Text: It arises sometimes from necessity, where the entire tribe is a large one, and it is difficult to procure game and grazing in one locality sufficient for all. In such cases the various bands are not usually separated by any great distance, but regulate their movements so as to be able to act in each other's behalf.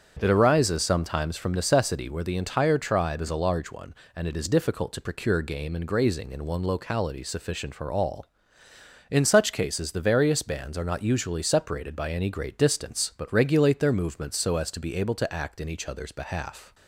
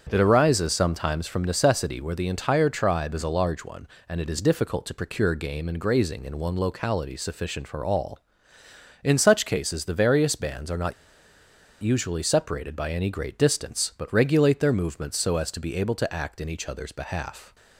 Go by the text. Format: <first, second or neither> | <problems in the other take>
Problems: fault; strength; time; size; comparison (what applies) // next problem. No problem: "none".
first | starts louder than the rest; strong; until 1.1 s; 7.5 dB; strong in the first // pauses between "not" and "usually"; noticeable; at 10.9 s; 0.89 s long